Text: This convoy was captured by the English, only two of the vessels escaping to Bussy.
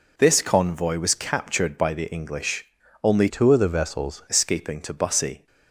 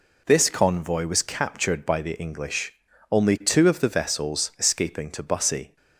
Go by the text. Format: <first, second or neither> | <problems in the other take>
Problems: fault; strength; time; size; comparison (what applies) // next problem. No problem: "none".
second | changes voice from "two" to "vessels"; from 3.2 to 4.2 s; 1.0 s long